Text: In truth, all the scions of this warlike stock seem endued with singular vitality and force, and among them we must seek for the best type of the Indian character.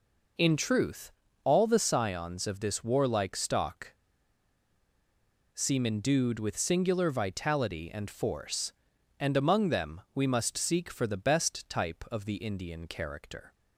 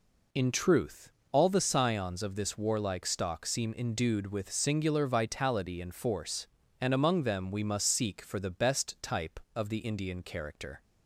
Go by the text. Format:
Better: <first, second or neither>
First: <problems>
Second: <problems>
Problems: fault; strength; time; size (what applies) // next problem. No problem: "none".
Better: second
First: pauses between "stock" and "seem"; strong; at 3.9 s; 1.6 s long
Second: none